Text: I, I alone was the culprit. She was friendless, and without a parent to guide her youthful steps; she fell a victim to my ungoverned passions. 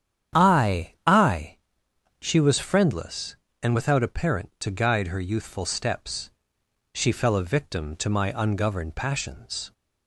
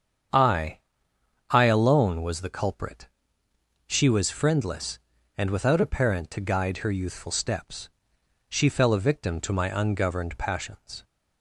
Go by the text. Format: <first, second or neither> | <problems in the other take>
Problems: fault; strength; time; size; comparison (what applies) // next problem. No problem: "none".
second | starts louder than the rest; strong; until 1.4 s; 9 dB; strong in the second // skips "alone was the culprit"; at 1.8 s